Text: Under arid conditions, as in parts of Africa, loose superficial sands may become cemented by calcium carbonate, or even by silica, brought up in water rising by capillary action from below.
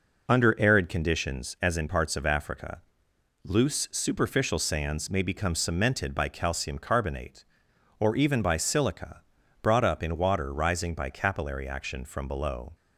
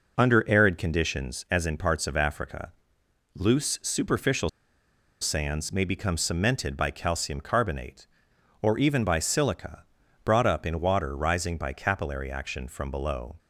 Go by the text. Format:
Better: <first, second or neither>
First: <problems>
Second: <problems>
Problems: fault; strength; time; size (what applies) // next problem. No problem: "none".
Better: first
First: none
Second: pauses between "superficial" and "sands"; noticeable; at 4.4 s; 0.71 s long